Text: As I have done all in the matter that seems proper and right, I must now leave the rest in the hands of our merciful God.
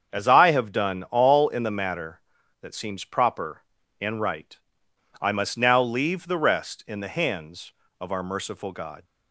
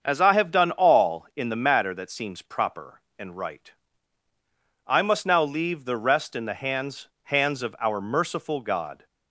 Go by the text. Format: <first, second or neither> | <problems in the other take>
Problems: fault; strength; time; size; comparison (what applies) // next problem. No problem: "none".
first | starts louder than the rest; until 1.0 s; 7 dB; also in the first // says "hands" twice; at 7.2 s